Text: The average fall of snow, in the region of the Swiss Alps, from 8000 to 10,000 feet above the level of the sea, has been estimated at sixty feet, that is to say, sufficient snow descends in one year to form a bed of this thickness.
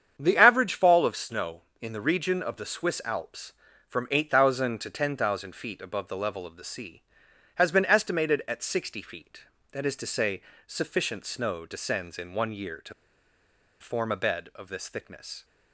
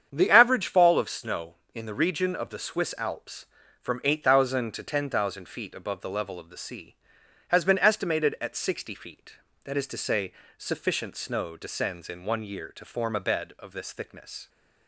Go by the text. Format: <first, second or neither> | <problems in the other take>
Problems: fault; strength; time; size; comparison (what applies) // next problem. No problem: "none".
second | starts louder than the rest; strong; until 1.2 s; 8 dB; strong in the second // pauses between "to" and "form"; noticeable; at 12.9 s; 0.87 s long